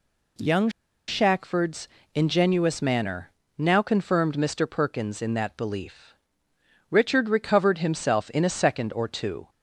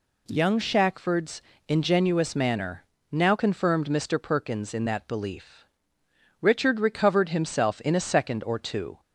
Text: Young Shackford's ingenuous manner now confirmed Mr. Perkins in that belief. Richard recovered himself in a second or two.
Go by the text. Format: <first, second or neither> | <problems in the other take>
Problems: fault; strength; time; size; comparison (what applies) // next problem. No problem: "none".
second | pauses between "Young" and "Shackford's"; at 0.6 s; 0.38 s long // pauses between "Shackford's" and "ingenuous"; slight; at 1.8 s; 0.28 s long; slight in the second // pauses between "manner" and "now"; slight; at 3.2 s; 0.30 s long; slight in the second